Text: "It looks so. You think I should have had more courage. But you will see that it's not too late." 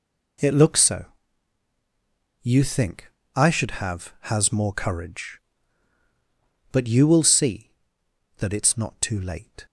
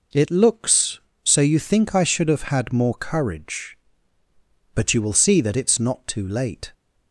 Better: second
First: pauses between "think" and "I"; slight; at 3.1 s; 0.24 s long // says "has" for "had"; at 4.2 s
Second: none

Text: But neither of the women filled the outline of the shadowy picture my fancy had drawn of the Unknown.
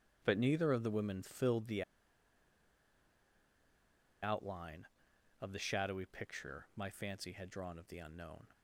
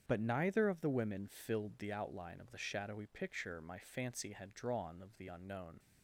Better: second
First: starts louder than the rest; strong; until 1.2 s; 10 dB // pauses between "the" and "outline"; strong; at 1.8 s; 2.4 s long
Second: starts louder than the rest; strong; until 1.0 s; 8 dB

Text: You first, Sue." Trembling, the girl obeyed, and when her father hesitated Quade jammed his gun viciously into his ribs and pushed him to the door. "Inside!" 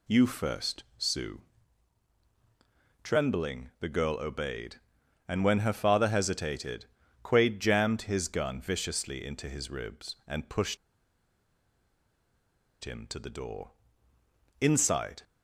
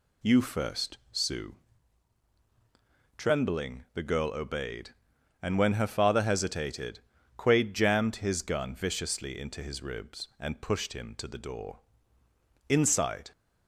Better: second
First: pauses between "hesitated" and "Quade"; at 6.8 s; 0.40 s long // pauses between "pushed" and "him"; strong; at 10.7 s; 2.0 s long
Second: pauses between "hesitated" and "Quade"; at 6.9 s; 0.40 s long

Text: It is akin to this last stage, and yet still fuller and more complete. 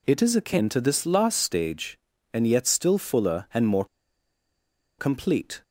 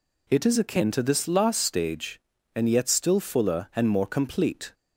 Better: second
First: pauses between "more" and "complete"; at 3.8 s; 1.1 s long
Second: none

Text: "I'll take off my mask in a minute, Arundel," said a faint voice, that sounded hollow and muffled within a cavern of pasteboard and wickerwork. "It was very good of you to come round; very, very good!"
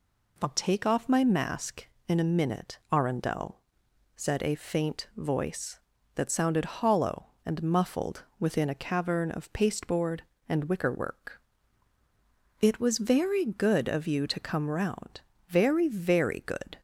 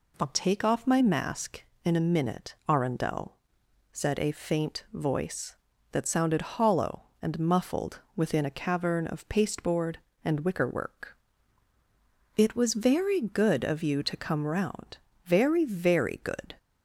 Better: neither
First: pauses between "muffled" and "within"; slight; at 8.2 s; 0.16 s long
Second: pauses between "muffled" and "within"; slight; at 7.9 s; 0.16 s long

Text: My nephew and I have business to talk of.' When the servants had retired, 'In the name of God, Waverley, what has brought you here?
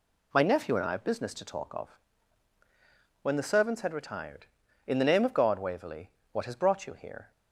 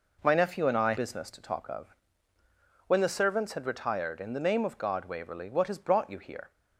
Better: first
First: none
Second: skips "have"; at 0.9 s

